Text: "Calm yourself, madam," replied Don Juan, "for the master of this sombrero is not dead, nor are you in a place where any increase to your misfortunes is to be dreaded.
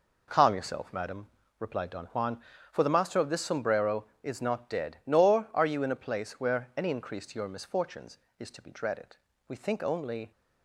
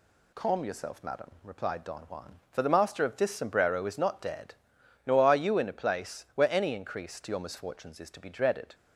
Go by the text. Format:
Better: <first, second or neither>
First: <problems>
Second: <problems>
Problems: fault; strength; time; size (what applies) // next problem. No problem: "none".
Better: second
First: goes on to say "We think only"; noticeable; from 9.4 s on; 0.84 s long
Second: none